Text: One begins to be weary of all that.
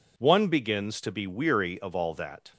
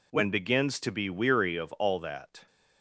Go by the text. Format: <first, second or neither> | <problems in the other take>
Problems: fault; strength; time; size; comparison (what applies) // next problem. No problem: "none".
first | says "When" for "One"; at 0.1 s